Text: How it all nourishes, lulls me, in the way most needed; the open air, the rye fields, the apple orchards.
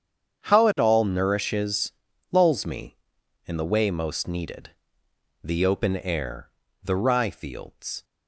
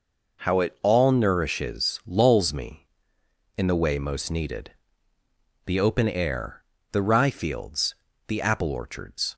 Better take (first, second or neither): second